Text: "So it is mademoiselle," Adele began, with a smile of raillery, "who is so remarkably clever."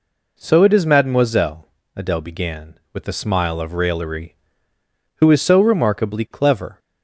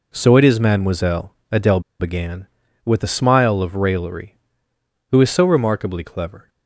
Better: first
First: none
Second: pauses between "Adele" and "began"; slight; at 1.7 s; 0.20 s long

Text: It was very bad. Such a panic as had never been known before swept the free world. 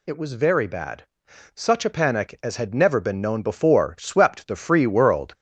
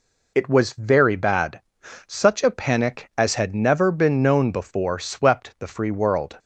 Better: second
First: gets louder; slight; throughout; 3.5 dB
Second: none

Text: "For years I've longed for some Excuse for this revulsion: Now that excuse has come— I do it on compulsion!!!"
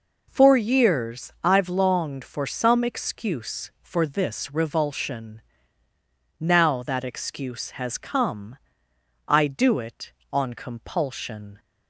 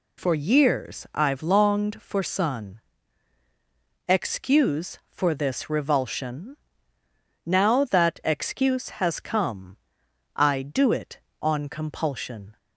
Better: first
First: none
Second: says "sun" for "some"; at 2.2 s

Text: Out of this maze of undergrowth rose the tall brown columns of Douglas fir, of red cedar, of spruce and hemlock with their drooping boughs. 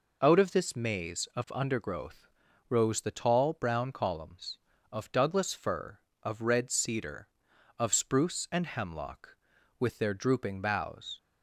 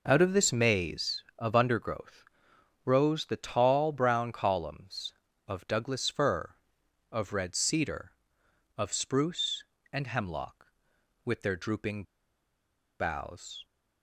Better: first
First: pauses between "undergrowth" and "rose"; at 2.2 s; 0.42 s long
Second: pauses between "undergrowth" and "rose"; noticeable; at 2.2 s; 0.62 s long // pauses between "drooping" and "boughs"; noticeable; at 12.0 s; 0.95 s long

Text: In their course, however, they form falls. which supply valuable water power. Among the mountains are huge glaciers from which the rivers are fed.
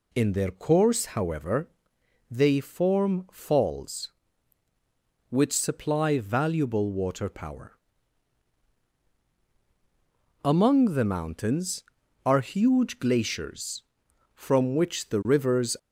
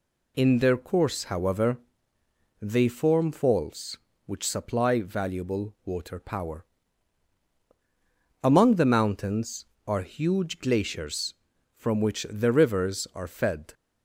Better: second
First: stops before "are fed"; at 15.7 s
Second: none

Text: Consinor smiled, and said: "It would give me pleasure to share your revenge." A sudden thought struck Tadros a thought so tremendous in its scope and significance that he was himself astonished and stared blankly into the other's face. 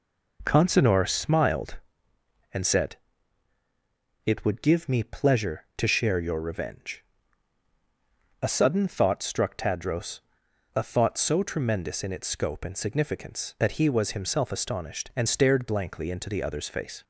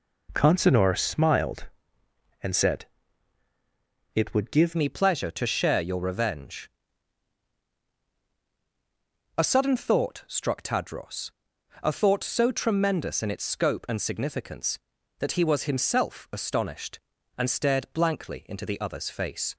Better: first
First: pauses between "Tadros" and "a"; noticeable; at 10.2 s; 0.54 s long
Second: changes voice at "me"; from 4.7 s on; 14.8 s long // pauses between "Tadros" and "a"; noticeable; at 11.3 s; 0.50 s long

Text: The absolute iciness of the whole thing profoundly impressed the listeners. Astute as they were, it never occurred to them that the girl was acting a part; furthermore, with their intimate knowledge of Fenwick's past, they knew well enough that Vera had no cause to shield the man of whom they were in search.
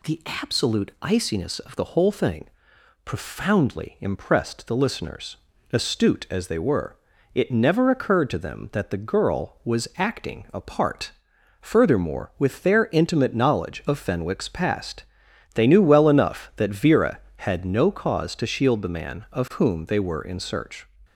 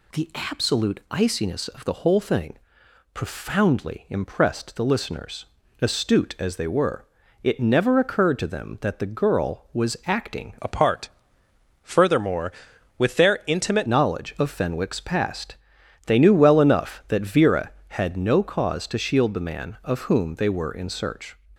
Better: first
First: pauses between "thing" and "profoundly"; noticeable; at 2.4 s; 0.58 s long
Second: pauses between "thing" and "profoundly"; noticeable; at 2.5 s; 0.58 s long // changes voice from "a" to "intimate"; from 10.5 to 13.8 s; 3.3 s long

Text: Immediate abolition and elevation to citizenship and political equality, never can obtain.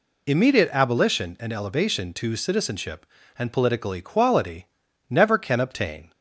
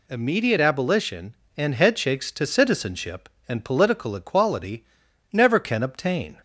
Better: first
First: none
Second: says "headshakes" for "elevation"; at 1.7 s

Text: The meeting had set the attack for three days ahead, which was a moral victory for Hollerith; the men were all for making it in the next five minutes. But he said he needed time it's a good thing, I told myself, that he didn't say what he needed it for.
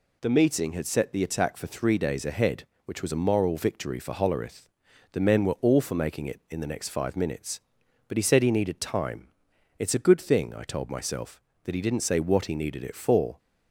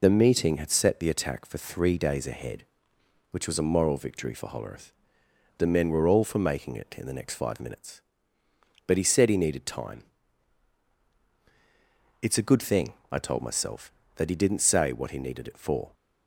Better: first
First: pauses between "time" and "it's"; noticeable; at 9.2 s; 0.52 s long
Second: loses the start of "The"; at 0.0 s; 35 ms // pauses between "time" and "it's"; strong; at 10.0 s; 2.1 s long

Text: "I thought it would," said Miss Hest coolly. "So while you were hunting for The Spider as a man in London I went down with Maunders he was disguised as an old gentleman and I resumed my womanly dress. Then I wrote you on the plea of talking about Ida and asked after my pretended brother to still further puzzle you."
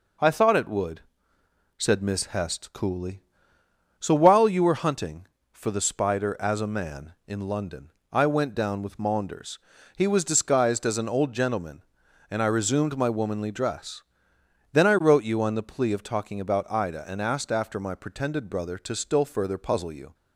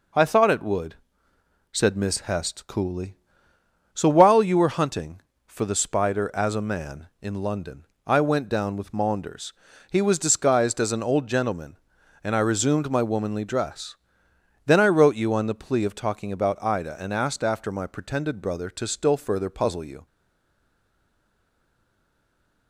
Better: first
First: pauses between "London" and "I"; slight; at 7.9 s; 0.18 s long // pauses between "Maunders" and "he"; slight; at 9.6 s; 0.36 s long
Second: pauses between "London" and "I"; slight; at 7.8 s; 0.18 s long // pauses between "Maunders" and "he"; slight; at 9.5 s; 0.36 s long // stays silent after the last word; strong; from 20.0 s on; 2.6 s long

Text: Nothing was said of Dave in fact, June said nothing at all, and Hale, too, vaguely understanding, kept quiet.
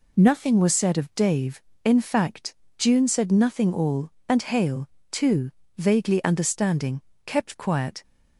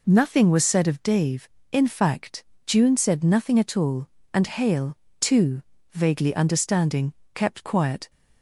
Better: second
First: skips "at"; at 3.7 s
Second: none

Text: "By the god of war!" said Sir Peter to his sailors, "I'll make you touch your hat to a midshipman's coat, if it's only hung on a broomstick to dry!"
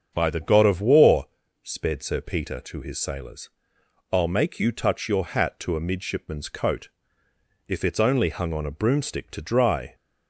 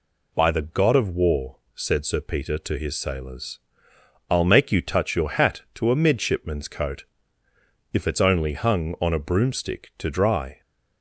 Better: second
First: starts louder than the rest; strong; until 1.1 s; 7 dB // says "sped" for "said"; at 1.6 s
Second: none

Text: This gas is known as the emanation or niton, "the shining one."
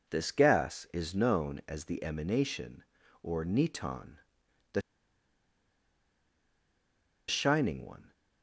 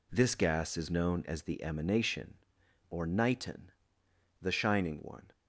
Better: second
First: pauses between "the" and "shining"; strong; at 4.7 s; 2.4 s long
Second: none

